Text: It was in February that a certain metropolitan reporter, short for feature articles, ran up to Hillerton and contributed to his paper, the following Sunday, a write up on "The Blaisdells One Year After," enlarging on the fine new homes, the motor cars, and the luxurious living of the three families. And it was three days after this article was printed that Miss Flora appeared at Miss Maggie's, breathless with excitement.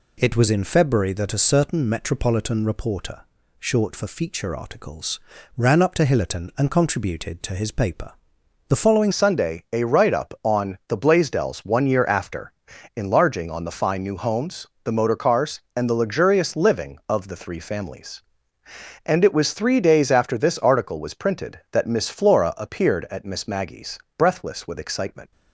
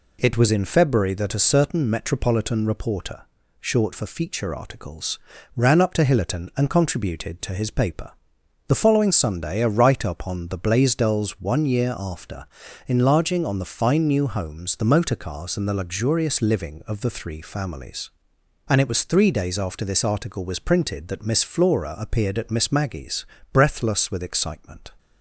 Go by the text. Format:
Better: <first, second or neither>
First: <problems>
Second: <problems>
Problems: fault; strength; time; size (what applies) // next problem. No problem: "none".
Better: second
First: changes voice at "Sunday"; from 9.1 s on; 16.2 s long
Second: none